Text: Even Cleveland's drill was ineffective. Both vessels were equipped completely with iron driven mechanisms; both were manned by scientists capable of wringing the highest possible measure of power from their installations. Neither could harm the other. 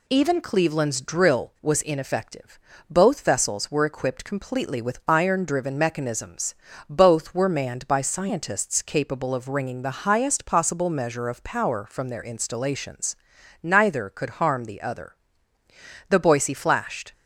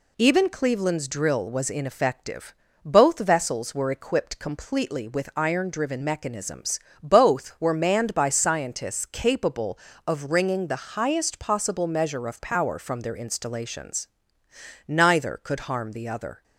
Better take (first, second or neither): second